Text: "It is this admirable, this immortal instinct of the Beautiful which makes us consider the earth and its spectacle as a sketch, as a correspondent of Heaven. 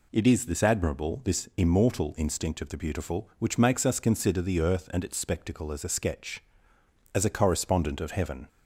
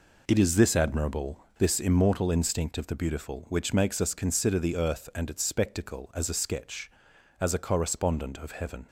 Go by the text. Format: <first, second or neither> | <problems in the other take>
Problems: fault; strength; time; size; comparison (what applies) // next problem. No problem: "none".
first | gets quieter; strong; throughout; 8.5 dB